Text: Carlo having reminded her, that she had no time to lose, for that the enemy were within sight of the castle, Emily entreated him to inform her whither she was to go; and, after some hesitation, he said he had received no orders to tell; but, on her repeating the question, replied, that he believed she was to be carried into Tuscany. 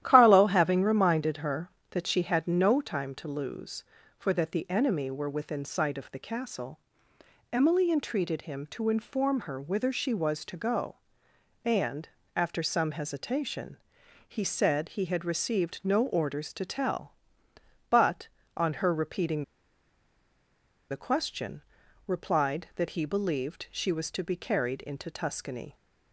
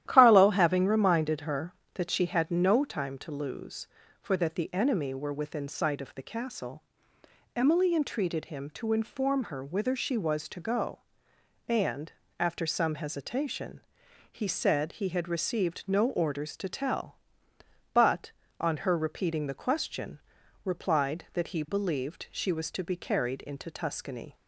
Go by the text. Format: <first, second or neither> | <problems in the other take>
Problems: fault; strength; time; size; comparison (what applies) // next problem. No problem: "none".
second | starts louder than the rest; strong; until 1.0 s; 12 dB; strong in the second // pauses between "repeating" and "the"; strong; at 19.4 s; 1.4 s long